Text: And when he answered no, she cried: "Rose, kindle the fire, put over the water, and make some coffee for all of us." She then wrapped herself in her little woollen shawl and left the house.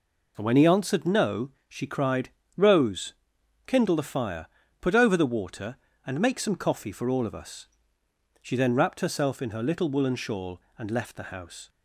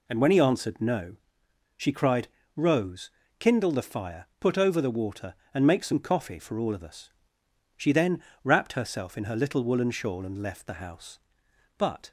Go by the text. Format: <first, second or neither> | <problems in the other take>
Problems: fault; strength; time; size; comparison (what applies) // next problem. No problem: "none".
first | pauses between "then" and "wrapped"; slight; at 8.2 s; 0.20 s long // goes on to say "But"; slight; from 11.7 s on; 0.32 s long